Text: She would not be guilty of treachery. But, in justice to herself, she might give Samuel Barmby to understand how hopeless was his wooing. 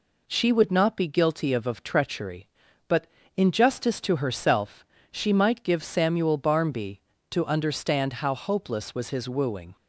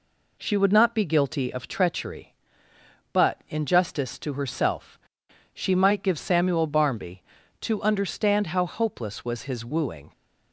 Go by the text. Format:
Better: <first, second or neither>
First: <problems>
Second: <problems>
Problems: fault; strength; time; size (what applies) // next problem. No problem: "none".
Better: second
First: says "of" twice; at 1.6 s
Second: none